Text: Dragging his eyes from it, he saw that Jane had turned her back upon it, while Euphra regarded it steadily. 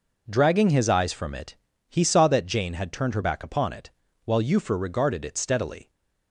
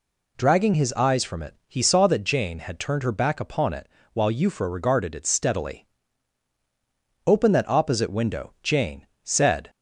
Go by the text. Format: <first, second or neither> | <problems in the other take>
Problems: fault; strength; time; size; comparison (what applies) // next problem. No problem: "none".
first | goes on to say "Open that opposite window Jane said"; strong; from 7.2 s on; 2.4 s long